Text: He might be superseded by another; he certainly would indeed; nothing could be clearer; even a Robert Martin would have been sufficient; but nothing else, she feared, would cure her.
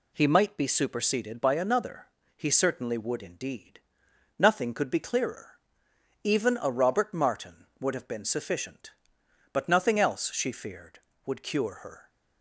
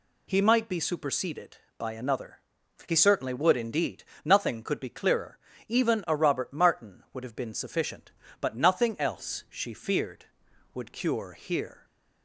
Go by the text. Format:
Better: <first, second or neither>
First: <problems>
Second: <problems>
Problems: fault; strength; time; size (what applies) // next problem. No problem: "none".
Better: first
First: none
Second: says "here" for "her"; at 11.3 s